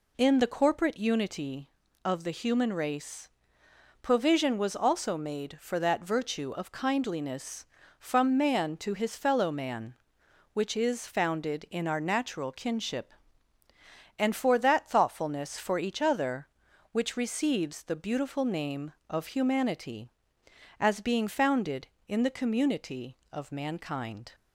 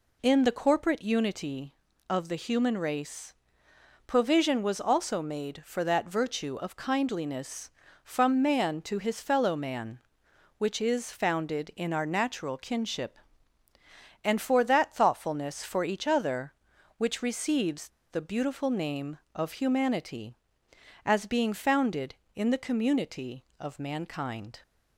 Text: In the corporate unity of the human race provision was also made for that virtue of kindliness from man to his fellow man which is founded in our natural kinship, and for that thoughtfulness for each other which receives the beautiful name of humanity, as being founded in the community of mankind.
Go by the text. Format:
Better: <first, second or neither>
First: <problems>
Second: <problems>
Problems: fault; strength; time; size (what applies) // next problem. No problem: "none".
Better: first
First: pauses between "race" and "provision"; noticeable; at 3.2 s; 0.72 s long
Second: pauses between "race" and "provision"; noticeable; at 3.3 s; 0.72 s long // pauses between "receives" and "the"; slight; at 17.8 s; 0.22 s long